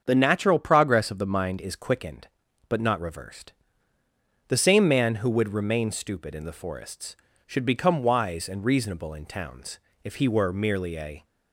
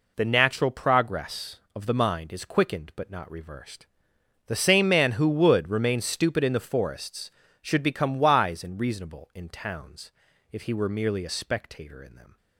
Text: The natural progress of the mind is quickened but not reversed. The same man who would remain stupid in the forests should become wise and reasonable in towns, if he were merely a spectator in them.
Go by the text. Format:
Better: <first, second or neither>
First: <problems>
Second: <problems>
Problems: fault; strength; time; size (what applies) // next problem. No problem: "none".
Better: second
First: starts louder than the rest; until 1.0 s; 7 dB // stops before "spectator in them"; at 11.2 s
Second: none